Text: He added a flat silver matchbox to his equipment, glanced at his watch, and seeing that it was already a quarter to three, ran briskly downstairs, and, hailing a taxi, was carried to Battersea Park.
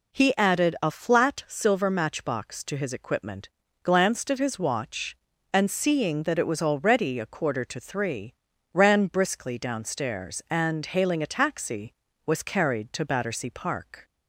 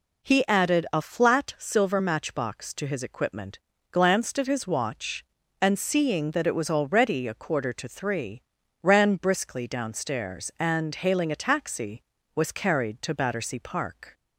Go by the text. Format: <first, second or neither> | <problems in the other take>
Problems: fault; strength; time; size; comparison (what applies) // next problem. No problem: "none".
neither | none